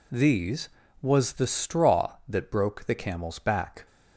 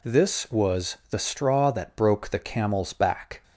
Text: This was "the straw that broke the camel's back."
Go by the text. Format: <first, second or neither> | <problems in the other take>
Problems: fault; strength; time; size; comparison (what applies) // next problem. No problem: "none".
second | says "These" for "This"; at 0.1 s